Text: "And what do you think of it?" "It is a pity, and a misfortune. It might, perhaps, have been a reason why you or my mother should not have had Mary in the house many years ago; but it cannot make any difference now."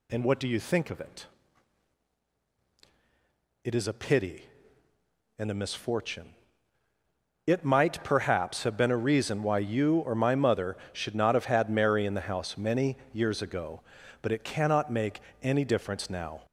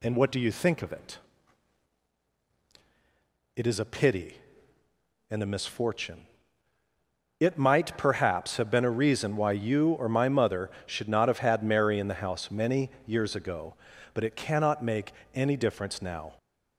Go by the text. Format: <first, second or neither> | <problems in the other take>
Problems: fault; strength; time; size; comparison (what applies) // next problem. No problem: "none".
second | gets louder; noticeable; throughout; 4 dB // pauses between "many" and "years"; slight; at 12.9 s; 0.16 s long; slight in the second // pauses between "make" and "any"; slight; at 15.2 s; 0.22 s long; slight in the second